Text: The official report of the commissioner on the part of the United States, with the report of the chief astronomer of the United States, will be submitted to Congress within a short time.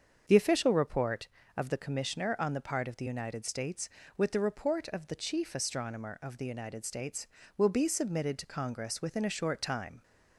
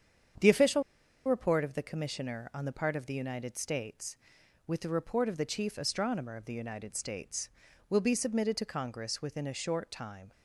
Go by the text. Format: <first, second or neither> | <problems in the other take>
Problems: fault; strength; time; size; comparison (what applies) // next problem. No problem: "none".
first | starts louder than the rest; strong; until 1.8 s; 8 dB; also in the first // pauses between "official" and "report"; at 0.8 s; 0.44 s long